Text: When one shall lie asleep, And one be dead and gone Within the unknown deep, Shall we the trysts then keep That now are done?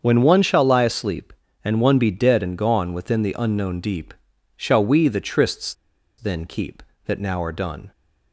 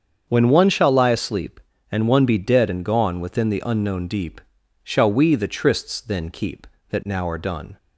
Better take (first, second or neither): second